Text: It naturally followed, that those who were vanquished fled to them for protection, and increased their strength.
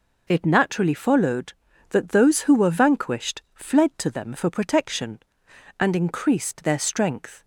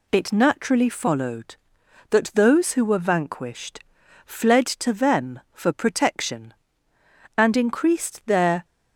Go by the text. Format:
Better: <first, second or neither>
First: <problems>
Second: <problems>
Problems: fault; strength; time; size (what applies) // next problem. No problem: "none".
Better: first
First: none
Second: pauses between "vanquished" and "fled"; at 3.8 s; 0.44 s long // stops before "strength"; at 8.6 s